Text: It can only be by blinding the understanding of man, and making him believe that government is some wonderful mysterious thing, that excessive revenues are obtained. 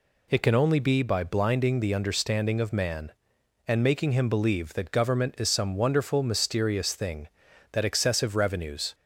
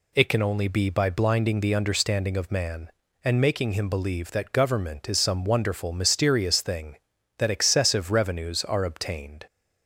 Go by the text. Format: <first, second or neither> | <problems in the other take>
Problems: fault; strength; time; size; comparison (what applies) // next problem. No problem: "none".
second | stops before "are obtained"; at 8.9 s